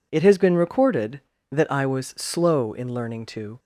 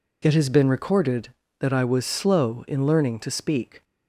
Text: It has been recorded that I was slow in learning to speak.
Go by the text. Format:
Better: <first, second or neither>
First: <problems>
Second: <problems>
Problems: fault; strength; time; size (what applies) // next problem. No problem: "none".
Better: second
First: stops before "speak"; at 3.5 s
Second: none